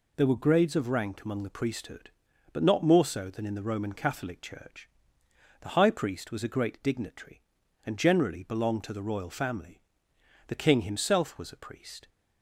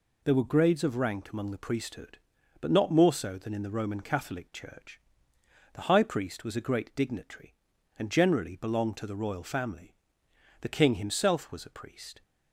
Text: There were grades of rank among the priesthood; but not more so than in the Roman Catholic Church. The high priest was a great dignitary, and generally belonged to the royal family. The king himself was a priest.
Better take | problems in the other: neither | none

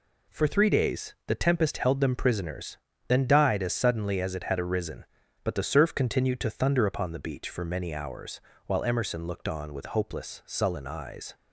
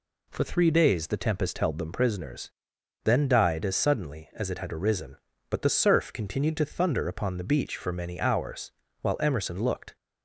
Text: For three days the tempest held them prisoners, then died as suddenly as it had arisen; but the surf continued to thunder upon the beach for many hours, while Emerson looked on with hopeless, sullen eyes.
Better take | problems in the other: first | stops before "on with hopeless sullen eyes"; at 9.9 s

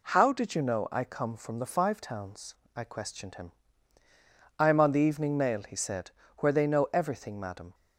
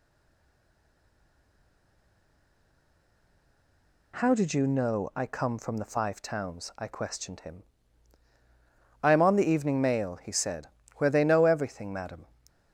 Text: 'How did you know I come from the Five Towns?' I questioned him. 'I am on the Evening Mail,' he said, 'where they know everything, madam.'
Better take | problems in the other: first | stays silent before the first word; strong; until 4.1 s; 4.1 s long

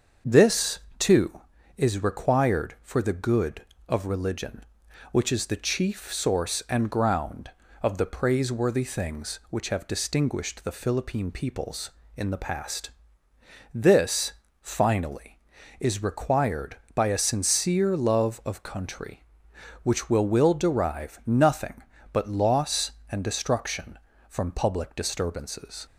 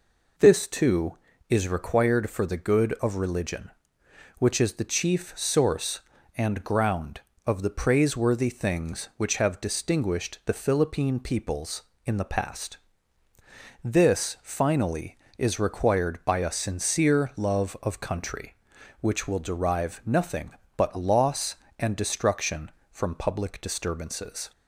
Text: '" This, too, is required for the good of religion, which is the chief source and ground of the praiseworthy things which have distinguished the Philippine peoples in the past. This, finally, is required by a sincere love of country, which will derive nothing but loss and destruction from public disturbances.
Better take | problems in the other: second | starts louder than the rest; until 1.4 s; 6.5 dB // says "will" twice; at 20.2 s

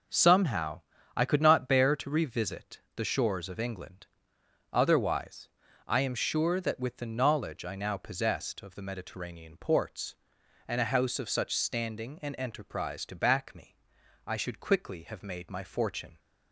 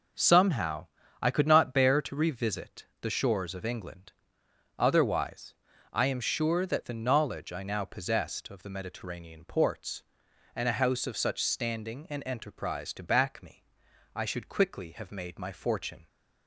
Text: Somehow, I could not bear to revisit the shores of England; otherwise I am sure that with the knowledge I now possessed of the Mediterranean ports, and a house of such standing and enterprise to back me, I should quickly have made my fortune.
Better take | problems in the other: first | pauses between "revisit" and "the"; slight; at 2.8 s; 0.16 s long; slight in the first // pauses between "otherwise" and "I"; slight; at 5.5 s; 0.36 s long; slight in the first // skips "with"; at 6.8 s

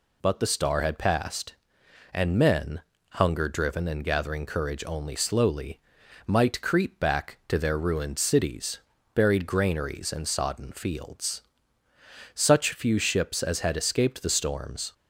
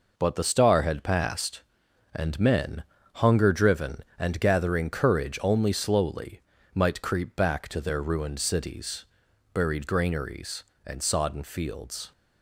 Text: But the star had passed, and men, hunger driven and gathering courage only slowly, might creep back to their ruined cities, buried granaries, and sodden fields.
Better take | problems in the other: second | goes on to say "Such few ships as had escaped the storms"; strong; from 12.3 s on; 2.5 s long

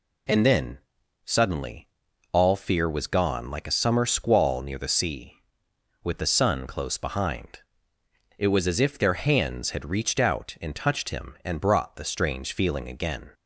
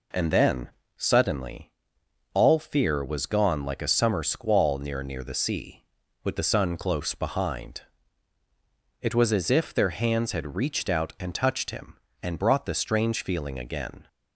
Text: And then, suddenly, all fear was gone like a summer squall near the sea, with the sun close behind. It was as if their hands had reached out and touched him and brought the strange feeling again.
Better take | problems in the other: first | says "near" twice; at 5.0 s

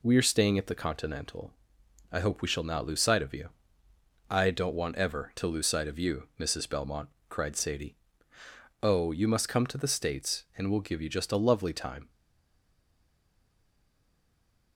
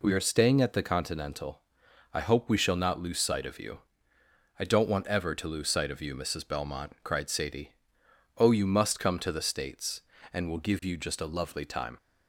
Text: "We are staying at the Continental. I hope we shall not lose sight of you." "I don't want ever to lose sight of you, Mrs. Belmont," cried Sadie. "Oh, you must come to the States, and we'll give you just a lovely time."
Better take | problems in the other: second | stays silent after the last word; strong; from 12.0 s on; 2.7 s long

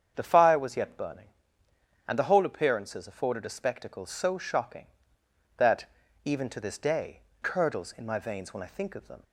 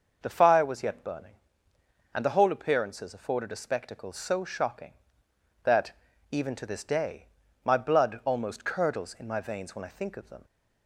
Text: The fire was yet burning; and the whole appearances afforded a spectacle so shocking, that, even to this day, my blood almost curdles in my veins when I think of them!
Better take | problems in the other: second | starts louder than the rest; strong; until 1.1 s; 7.5 dB; noticeable in the second // skips "my blood almost"; at 7.3 s

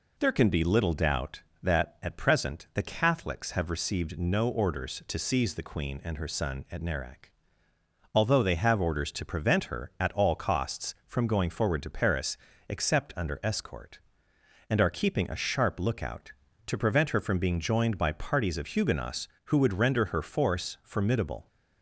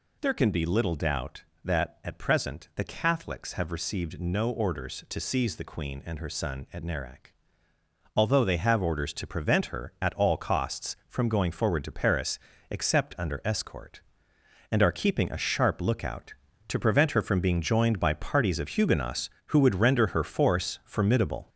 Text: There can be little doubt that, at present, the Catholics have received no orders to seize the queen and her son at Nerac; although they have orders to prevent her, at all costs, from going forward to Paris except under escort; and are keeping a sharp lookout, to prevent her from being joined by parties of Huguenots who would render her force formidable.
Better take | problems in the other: first | gets louder; noticeable; throughout; 5 dB // pauses between "Paris" and "except"; slight; at 12.3 s; 0.32 s long; slight in the first

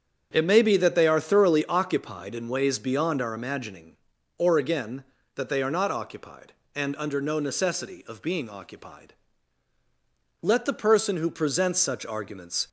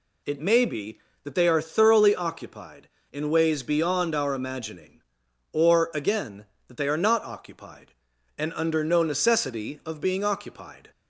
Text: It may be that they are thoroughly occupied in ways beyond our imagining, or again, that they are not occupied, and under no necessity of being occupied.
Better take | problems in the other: second | starts louder than the rest; strong; until 1.3 s; 7.5 dB // goes on to say "Let the person who presents such arguments"; strong; from 10.4 s on; 2.2 s long

